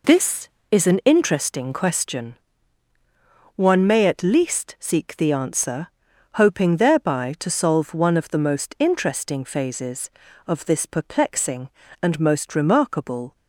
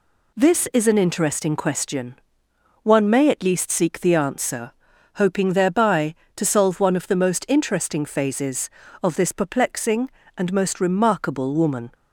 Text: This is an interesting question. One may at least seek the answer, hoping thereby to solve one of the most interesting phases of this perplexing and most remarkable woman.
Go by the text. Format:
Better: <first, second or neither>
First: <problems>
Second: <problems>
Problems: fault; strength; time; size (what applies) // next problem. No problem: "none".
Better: second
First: stops before "woman"; at 13.3 s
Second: none